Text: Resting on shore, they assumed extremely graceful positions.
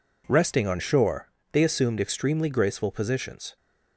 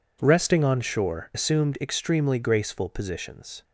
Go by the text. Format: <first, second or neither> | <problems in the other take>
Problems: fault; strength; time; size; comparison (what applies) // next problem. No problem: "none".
first | skips "they"; at 1.3 s